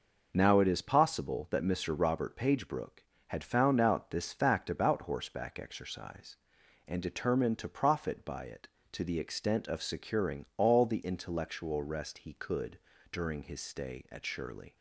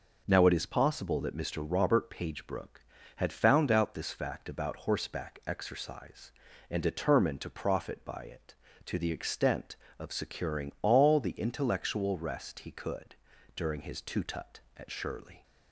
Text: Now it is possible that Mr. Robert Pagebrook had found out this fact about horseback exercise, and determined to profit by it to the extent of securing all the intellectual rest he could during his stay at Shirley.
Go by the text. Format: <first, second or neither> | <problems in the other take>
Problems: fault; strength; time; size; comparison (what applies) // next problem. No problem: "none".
first | pauses between "could" and "during"; at 13.1 s; 0.40 s long; slight in the first // says "tutut" for "stay"; at 14.0 s